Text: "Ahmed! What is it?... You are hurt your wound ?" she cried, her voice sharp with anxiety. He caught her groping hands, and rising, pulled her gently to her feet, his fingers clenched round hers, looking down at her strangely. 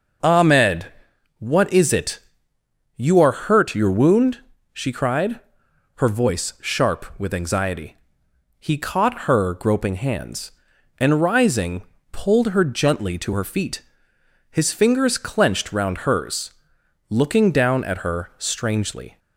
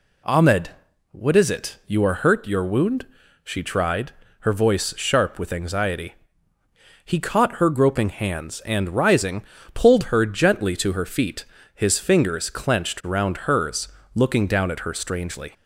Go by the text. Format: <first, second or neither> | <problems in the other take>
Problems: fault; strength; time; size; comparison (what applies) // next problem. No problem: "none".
first | says "tried" for "cried"; at 3.6 s